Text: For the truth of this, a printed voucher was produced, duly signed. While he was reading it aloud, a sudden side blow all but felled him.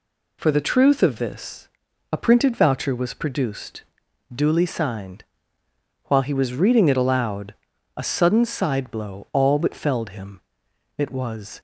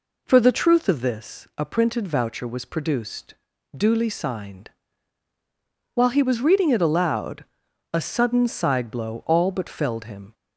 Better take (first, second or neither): second